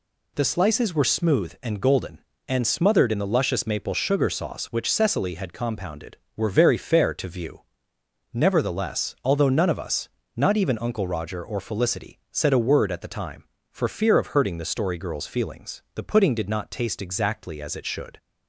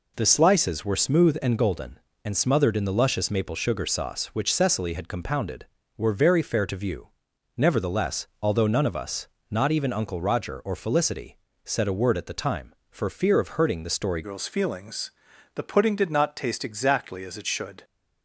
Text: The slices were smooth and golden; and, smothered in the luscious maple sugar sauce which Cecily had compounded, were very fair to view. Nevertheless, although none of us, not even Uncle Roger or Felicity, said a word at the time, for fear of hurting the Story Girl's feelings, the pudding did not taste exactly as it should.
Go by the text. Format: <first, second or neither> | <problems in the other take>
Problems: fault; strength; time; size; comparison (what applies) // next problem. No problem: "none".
first | changes voice at "Girl's"; from 14.2 s on; 3.6 s long